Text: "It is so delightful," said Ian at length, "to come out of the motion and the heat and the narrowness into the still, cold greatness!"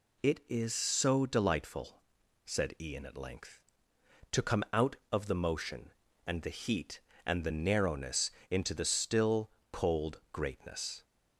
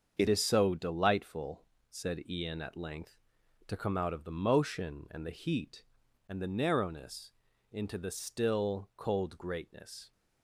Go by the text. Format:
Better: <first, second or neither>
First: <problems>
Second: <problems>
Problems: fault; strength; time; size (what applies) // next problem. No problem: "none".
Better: first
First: pauses between "narrowness" and "into"; slight; at 8.3 s; 0.18 s long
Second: starts louder than the rest; until 1.2 s; 6.5 dB // changes voice at "is"; from 0.2 s on; 9.9 s long // pauses between "narrowness" and "into"; at 7.3 s; 0.40 s long